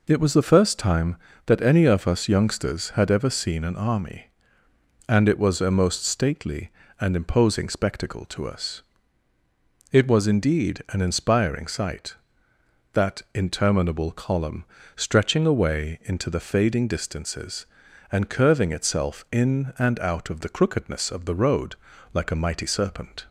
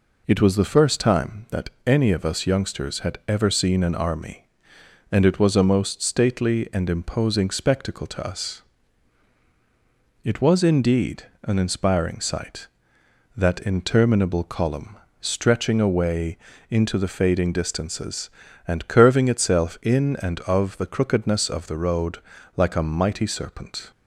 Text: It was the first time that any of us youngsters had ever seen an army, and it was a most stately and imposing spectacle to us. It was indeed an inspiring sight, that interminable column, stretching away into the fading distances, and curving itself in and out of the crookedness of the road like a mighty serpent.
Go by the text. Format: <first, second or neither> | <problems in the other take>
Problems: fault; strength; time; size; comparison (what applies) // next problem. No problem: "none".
first | pauses between "that" and "any"; slight; at 1.6 s; 0.16 s long // pauses between "indeed" and "an"; slight; at 11.2 s; 0.18 s long // pauses between "away" and "into"; slight; at 16.3 s; 0.32 s long // skips "out"; at 20.4 s // pauses between "road" and "like"; at 22.1 s; 0.40 s long; slight in the first